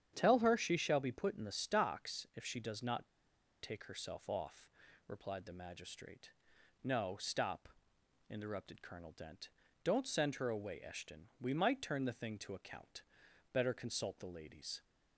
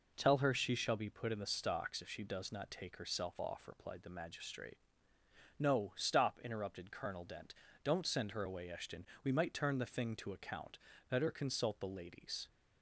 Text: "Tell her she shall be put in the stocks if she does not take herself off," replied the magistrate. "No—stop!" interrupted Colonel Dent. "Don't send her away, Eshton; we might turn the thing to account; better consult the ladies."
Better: second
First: starts louder than the rest; strong; until 1.1 s; 9 dB // pauses between "not" and "take"; noticeable; at 3.0 s; 0.55 s long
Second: none

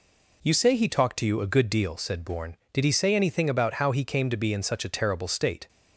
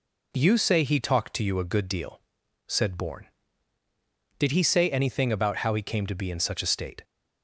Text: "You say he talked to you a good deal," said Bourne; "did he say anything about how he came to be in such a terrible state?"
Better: first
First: none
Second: skips "terrible"; at 6.6 s

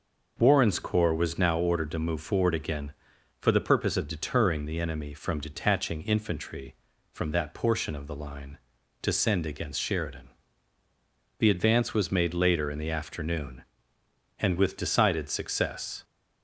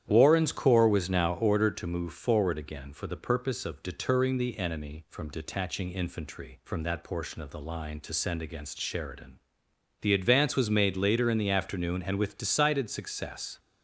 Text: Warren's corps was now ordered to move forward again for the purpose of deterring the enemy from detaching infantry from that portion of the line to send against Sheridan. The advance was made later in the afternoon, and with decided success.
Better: first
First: none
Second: starts louder than the rest; strong; until 1.5 s; 10.5 dB

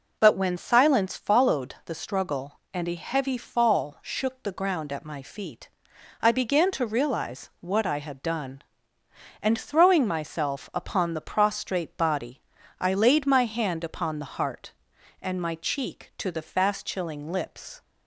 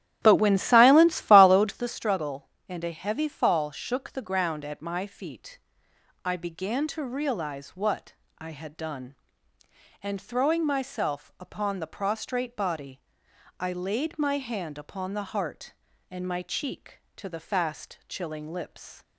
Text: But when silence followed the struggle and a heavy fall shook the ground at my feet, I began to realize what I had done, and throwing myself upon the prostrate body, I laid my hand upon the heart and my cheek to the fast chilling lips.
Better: first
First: none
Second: starts louder than the rest; strong; until 2.0 s; 11.5 dB // pauses between "what" and "I"; slight; at 8.1 s; 0.24 s long

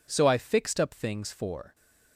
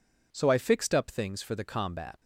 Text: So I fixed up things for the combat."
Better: second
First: stops before "the combat"; at 1.7 s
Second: none

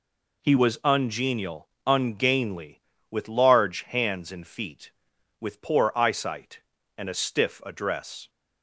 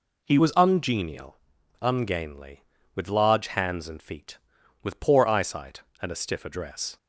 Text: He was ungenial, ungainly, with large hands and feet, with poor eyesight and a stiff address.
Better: first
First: none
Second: changes voice at "was"; from 0.3 s on; 6.6 s long

